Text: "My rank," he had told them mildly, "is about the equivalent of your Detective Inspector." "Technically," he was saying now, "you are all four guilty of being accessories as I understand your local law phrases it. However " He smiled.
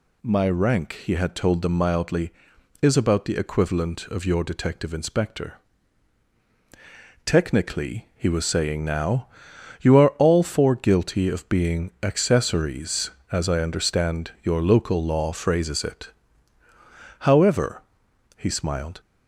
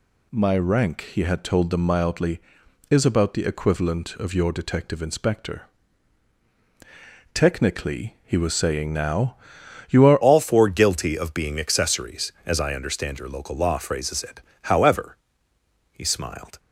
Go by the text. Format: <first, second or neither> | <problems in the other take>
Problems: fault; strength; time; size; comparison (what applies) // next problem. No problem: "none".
first | changes voice at "all"; from 10.2 s on; 6.3 s long